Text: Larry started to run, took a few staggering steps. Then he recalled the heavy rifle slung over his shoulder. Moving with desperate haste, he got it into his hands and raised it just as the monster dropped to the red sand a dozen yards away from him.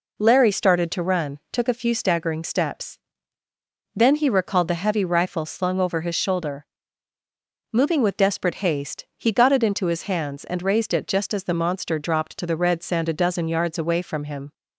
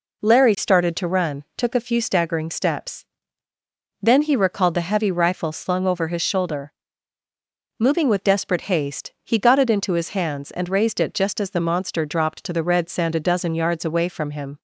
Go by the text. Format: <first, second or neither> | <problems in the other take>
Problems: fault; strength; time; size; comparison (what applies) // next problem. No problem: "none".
neither | none